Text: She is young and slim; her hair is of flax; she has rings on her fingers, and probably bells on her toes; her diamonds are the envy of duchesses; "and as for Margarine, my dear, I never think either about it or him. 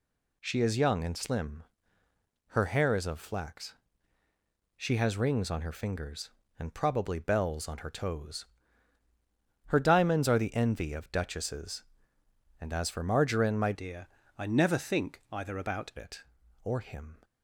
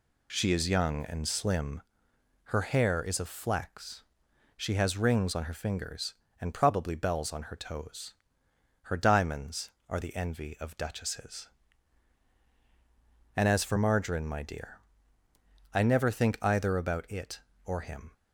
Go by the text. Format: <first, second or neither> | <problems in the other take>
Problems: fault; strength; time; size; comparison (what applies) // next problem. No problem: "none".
second | changes voice from "dear" to "about"; from 13.7 to 15.9 s; 2.2 s long